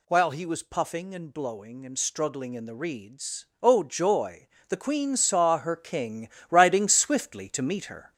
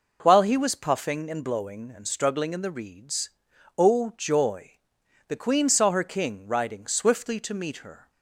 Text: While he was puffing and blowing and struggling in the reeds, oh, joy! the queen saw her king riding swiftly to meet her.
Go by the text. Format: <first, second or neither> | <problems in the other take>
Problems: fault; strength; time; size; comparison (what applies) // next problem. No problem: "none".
second | gets louder; noticeable; throughout; 4.5 dB // pauses between "king" and "riding"; slight; at 6.2 s; 0.22 s long